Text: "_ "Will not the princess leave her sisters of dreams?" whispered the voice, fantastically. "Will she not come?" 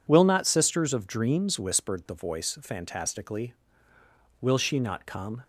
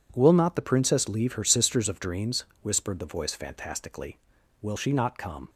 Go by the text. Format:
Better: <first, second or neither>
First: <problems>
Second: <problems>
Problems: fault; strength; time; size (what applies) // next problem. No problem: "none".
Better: second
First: skips "the princess leave her"; at 0.4 s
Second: none